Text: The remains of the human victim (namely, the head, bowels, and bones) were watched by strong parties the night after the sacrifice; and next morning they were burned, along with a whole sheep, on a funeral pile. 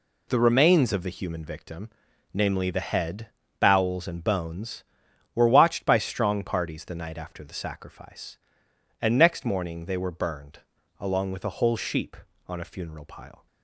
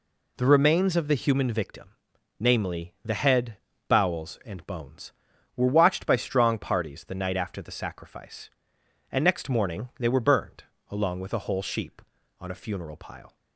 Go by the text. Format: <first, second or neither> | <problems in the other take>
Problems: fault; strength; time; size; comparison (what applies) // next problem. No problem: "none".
neither | none